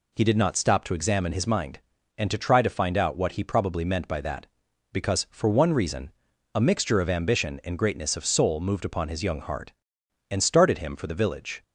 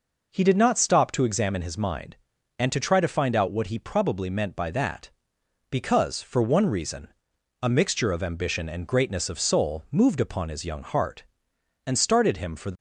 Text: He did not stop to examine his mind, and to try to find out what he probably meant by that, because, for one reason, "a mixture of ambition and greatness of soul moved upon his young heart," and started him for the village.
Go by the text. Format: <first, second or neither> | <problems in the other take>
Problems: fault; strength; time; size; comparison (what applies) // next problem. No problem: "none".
first | stops before "village"; at 12.7 s